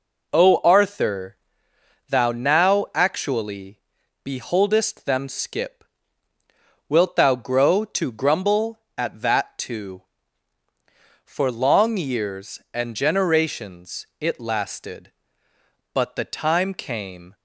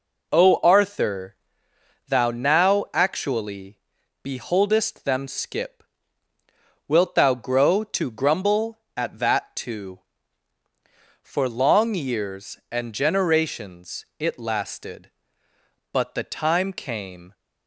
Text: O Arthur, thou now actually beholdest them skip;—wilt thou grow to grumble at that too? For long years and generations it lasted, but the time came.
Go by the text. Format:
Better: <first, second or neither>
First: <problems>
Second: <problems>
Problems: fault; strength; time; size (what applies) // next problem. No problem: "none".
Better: neither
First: pauses between "actually" and "beholdest"; at 3.7 s; 0.44 s long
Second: pauses between "actually" and "beholdest"; at 3.7 s; 0.44 s long